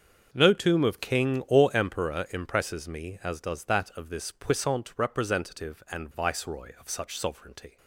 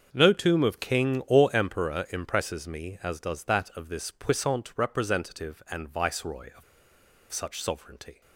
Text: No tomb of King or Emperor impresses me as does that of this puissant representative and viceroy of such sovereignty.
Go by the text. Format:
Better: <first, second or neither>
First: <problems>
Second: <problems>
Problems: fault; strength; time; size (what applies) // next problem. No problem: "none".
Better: first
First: starts louder than the rest; until 1.3 s; 6.5 dB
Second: starts louder than the rest; until 1.1 s; 6.5 dB // pauses between "of" and "such"; noticeable; at 6.6 s; 0.68 s long